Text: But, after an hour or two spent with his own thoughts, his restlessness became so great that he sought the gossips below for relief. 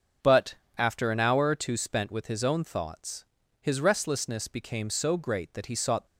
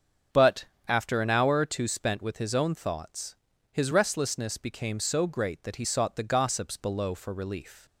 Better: second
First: starts louder than the rest; until 1.4 s; 6.5 dB // stops before "the gossips below for relief"; at 6.0 s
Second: starts louder than the rest; strong; until 1.5 s; 7 dB

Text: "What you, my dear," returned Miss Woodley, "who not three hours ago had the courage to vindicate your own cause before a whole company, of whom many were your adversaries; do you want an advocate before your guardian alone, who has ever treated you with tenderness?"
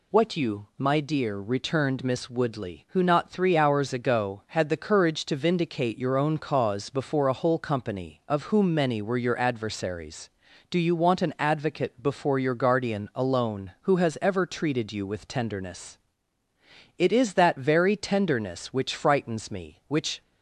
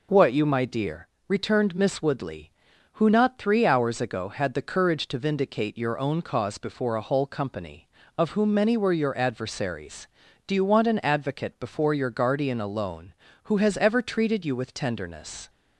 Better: second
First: goes on to say "It is that very tenderness which frightens me which"; strong; from 16.9 s on; 3.2 s long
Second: none

